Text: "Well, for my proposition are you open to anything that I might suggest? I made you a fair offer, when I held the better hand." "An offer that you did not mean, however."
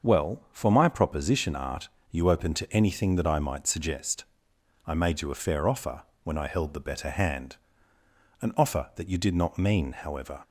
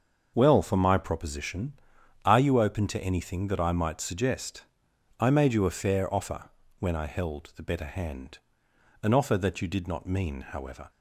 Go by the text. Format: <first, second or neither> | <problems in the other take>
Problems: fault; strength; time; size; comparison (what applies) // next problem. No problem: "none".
second | starts louder than the rest; until 1.1 s; 6.5 dB; also in the second // says "art" for "are"; at 1.5 s